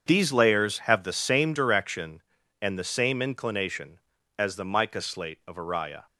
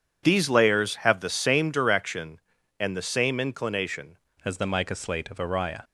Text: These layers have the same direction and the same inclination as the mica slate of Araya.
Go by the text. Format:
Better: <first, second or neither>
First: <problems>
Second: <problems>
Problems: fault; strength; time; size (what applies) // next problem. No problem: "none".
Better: first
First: none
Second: changes voice at "as"; from 4.4 s on; 1.4 s long